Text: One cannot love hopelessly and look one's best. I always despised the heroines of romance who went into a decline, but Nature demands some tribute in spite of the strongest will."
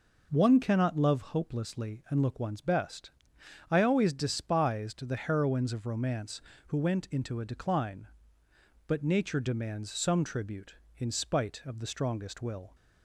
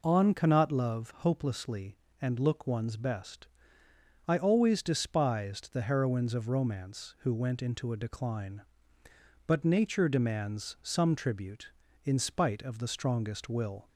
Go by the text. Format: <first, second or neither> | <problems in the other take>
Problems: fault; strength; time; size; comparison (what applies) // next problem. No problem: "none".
first | says "On" for "One"; at 0.0 s